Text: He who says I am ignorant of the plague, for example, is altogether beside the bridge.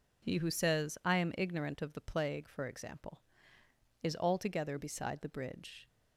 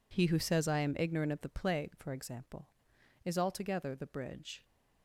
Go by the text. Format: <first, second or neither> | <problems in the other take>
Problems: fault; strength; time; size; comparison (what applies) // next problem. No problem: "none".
first | skips "beside"; at 3.9 s